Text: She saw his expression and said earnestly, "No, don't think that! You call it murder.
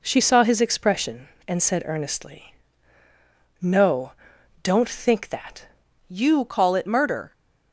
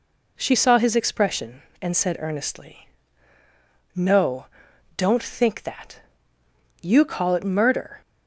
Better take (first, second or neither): second